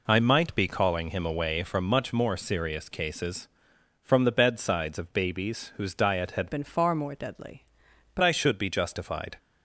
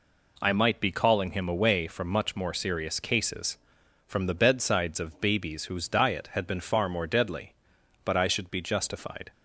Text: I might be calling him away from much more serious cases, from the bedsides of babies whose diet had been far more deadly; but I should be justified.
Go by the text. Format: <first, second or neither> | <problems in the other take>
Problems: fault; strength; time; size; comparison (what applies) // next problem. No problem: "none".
second | changes voice from "been" to "but"; from 6.4 to 8.2 s; 1.8 s long